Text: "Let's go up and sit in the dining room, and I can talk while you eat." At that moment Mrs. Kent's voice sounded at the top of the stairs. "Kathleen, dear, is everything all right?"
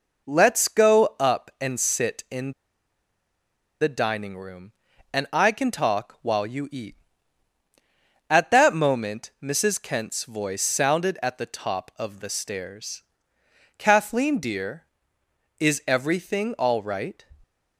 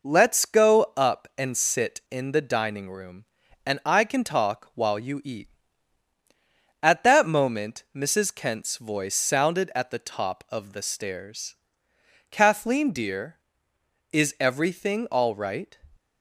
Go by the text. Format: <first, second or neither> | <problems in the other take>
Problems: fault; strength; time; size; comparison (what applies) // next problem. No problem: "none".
second | pauses between "in" and "the"; strong; at 2.5 s; 1.2 s long